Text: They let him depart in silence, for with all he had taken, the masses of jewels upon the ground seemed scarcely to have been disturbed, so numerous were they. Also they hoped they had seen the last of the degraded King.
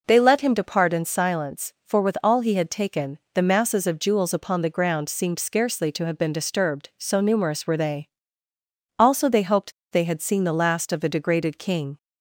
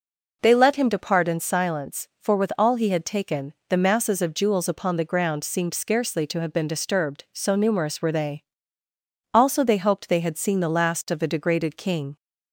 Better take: second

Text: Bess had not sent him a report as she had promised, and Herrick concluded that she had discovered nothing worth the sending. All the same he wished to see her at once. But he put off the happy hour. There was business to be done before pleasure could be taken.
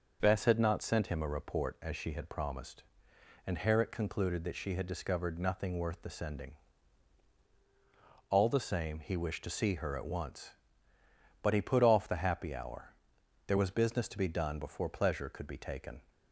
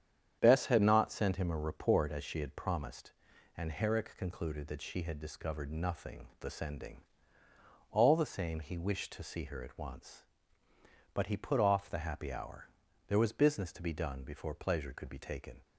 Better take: first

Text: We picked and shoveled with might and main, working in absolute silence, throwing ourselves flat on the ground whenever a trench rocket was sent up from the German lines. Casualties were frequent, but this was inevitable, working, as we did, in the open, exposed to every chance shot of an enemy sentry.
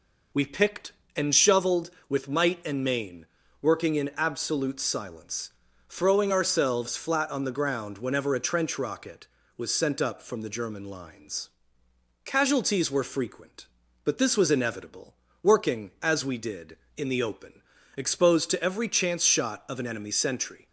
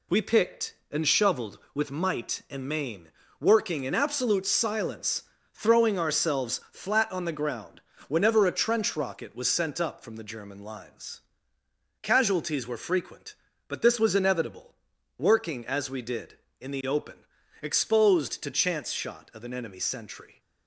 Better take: first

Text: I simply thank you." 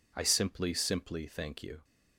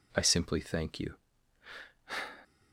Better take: second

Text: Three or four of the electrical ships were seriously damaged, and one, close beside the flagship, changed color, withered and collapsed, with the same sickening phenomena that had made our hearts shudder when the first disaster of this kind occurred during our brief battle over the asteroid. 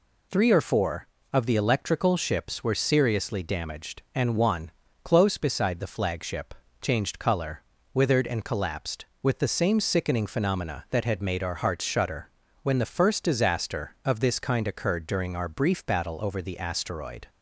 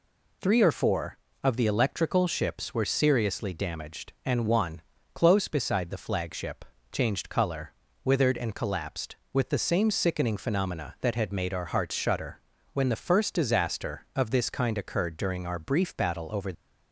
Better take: first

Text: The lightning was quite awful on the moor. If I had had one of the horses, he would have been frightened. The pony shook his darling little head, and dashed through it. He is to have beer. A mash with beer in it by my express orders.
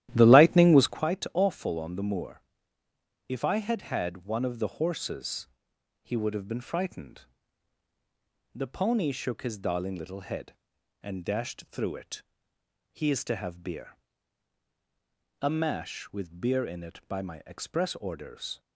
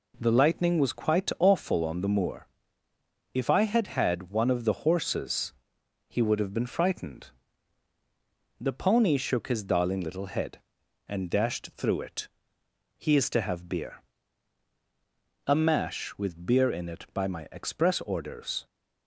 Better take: second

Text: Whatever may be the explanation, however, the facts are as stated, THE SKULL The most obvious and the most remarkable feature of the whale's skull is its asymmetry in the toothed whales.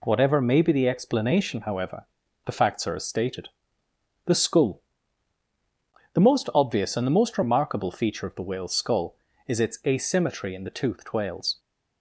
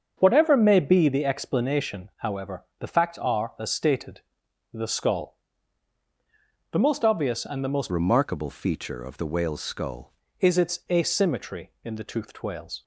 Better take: first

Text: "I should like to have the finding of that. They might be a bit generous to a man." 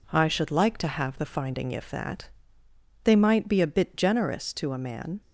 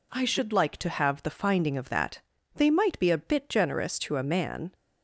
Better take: second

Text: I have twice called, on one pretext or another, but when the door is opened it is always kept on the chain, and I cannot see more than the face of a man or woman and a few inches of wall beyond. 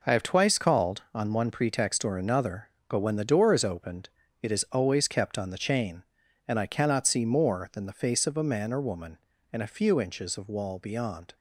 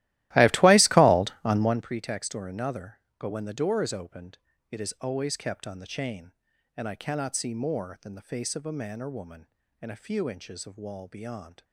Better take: first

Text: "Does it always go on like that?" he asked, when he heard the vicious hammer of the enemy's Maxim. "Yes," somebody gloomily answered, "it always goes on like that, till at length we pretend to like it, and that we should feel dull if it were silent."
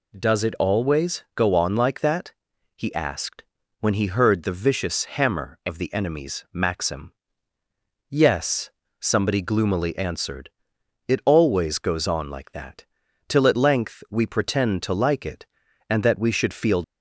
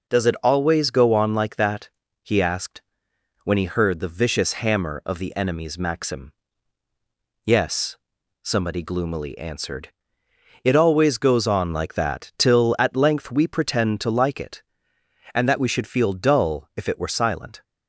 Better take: second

